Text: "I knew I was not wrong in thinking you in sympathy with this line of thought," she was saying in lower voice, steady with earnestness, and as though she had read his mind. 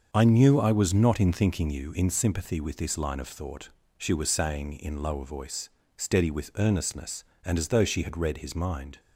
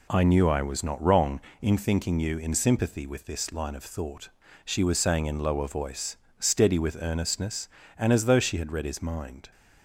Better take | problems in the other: second | starts louder than the rest; until 1.1 s; 6.5 dB // skips "wrong"; at 1.2 s

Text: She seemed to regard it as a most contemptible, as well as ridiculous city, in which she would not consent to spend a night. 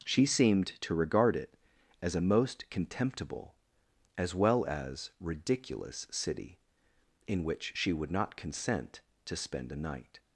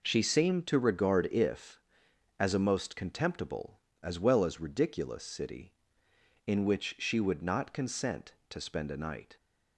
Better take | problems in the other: first | says "if" for "it"; at 1.3 s

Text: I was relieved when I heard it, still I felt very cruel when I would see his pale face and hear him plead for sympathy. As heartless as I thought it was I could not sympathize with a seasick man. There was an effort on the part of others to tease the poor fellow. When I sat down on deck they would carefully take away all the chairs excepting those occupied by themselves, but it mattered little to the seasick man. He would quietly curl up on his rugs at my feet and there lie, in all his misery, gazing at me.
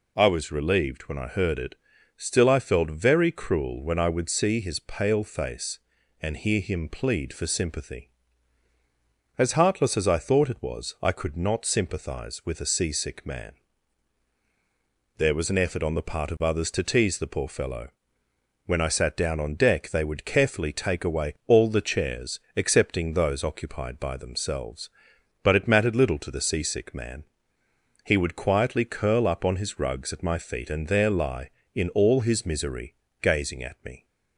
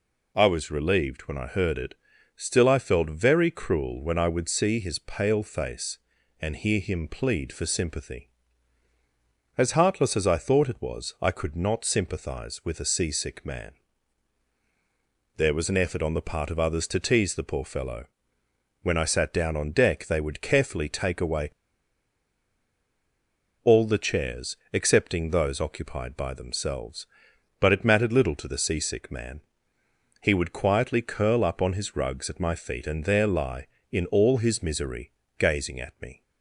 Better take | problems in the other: first | pauses between "away" and "all"; strong; at 21.5 s; 2.1 s long // pauses between "chairs" and "excepting"; slight; at 24.5 s; 0.16 s long; slight in the first

